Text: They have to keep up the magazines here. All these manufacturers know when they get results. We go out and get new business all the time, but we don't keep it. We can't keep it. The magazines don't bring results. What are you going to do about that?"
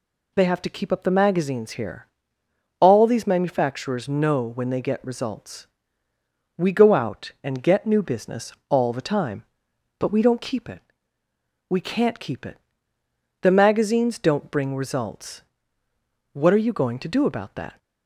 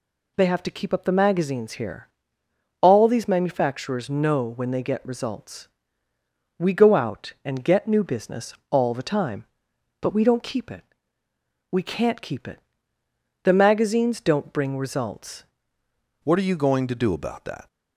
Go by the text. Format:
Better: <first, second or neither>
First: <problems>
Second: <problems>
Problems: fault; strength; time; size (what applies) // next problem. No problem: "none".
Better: first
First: pauses between "business" and "all"; slight; at 8.5 s; 0.16 s long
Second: pauses between "business" and "all"; slight; at 8.5 s; 0.16 s long // changes voice at "What"; from 16.2 s on; 1.4 s long